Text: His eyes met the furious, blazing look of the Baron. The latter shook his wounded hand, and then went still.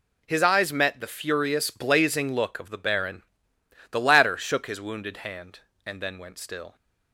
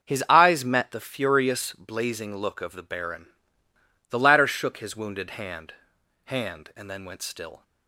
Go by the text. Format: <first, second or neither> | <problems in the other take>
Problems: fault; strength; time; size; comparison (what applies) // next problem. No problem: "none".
first | starts louder than the rest; until 1.0 s; 6.5 dB // says "hand" twice; at 6.2 s